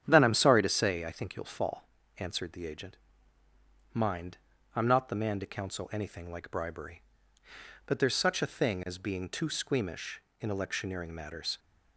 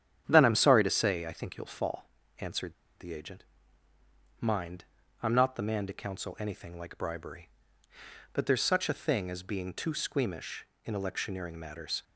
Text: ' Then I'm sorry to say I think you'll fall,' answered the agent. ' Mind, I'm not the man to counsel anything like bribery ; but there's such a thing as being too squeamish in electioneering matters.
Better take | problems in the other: first | starts louder than the rest; strong; until 1.2 s; 9 dB; strong in the first // pauses between "answered" and "the"; slight; at 2.7 s; 0.26 s long

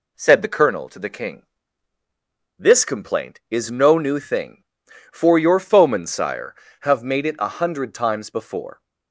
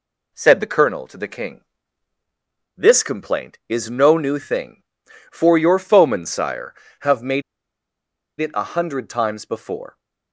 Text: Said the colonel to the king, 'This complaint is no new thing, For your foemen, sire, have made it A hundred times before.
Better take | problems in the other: first | pauses between "made" and "it"; at 7.4 s; 0.98 s long

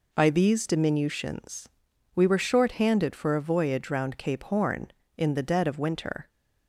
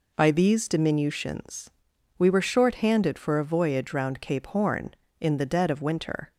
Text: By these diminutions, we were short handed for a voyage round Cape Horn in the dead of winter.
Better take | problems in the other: neither | none

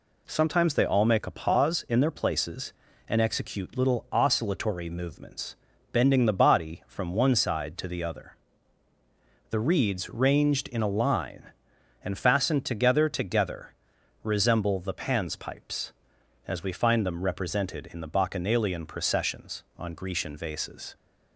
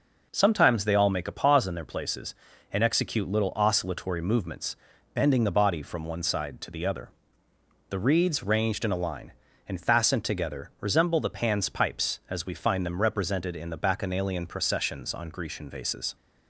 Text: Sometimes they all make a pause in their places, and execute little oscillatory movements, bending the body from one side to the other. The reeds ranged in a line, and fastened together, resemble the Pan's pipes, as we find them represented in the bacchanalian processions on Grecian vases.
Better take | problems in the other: second | says "together" twice; at 13.0 s

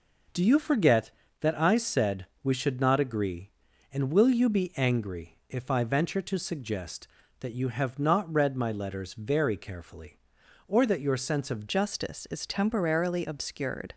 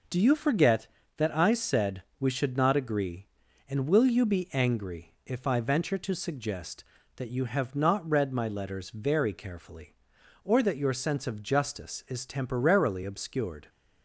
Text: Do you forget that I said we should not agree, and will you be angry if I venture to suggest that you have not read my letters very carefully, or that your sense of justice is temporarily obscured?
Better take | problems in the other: second | pauses between "said" and "we"; slight; at 2.2 s; 0.18 s long; slight in the second // changes voice at "justice"; from 11.6 s on; 2.3 s long

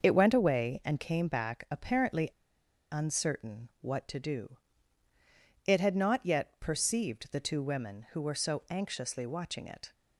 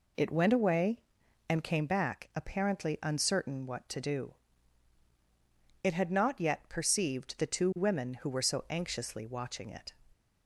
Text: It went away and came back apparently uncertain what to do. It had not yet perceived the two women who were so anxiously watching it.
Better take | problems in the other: second | starts louder than the rest; until 1.0 s; 6.5 dB // pauses between "apparently" and "uncertain"; noticeable; at 2.2 s; 0.62 s long

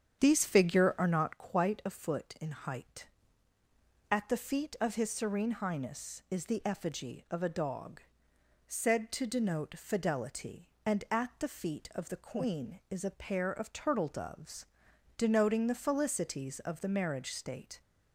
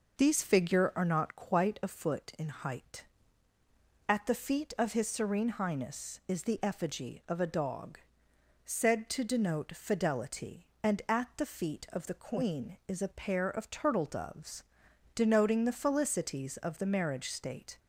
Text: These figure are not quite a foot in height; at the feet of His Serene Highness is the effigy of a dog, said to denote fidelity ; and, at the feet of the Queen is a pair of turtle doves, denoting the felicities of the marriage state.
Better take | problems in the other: second | starts louder than the rest; strong; until 1.3 s; 8 dB

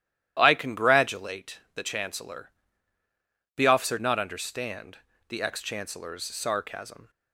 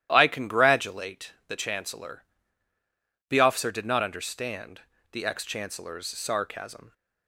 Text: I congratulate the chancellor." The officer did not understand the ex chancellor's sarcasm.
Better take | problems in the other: second | starts louder than the rest; strong; until 1.3 s; 12 dB; strong in the second // skips "did"; at 3.9 s // pauses between "understand" and "the"; slight; at 4.9 s; 0.30 s long; slight in the second

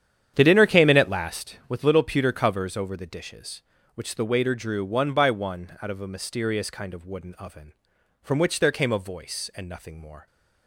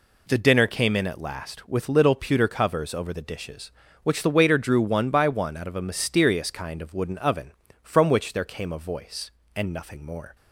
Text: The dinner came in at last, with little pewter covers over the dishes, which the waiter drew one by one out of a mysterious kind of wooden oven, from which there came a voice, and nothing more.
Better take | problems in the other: second | starts louder than the rest; strong; until 1.4 s; 9.5 dB

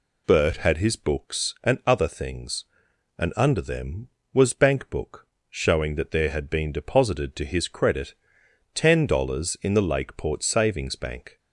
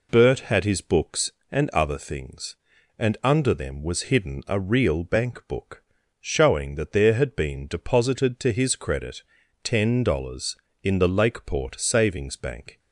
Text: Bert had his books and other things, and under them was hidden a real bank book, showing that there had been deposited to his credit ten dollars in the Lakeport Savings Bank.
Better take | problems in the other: second | skips "hidden a real"; at 4.5 s // pauses between "credit" and "ten"; noticeable; at 8.1 s; 0.58 s long; also in the second

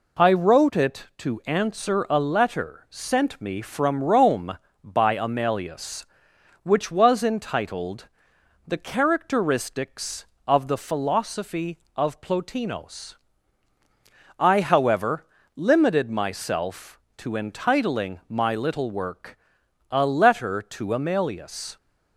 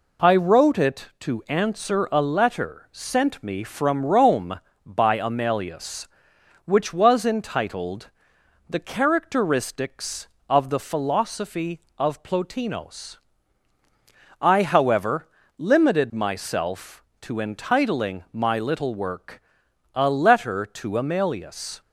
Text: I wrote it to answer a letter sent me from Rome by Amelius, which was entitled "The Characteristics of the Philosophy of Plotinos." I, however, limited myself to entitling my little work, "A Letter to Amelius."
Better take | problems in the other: neither | pauses between "entitled" and "The"; noticeable; the same in both

